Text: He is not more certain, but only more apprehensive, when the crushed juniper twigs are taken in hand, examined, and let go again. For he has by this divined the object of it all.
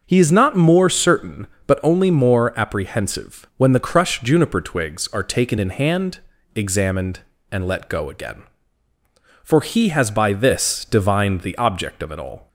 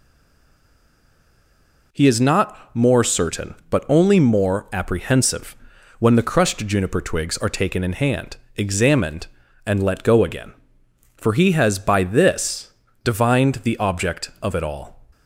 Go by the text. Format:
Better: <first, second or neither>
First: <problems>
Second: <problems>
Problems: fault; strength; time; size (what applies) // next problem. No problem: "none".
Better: first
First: none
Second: stays silent before the first word; noticeable; until 1.9 s; 1.9 s long // pauses between "this" and "divined"; slight; at 12.7 s; 0.32 s long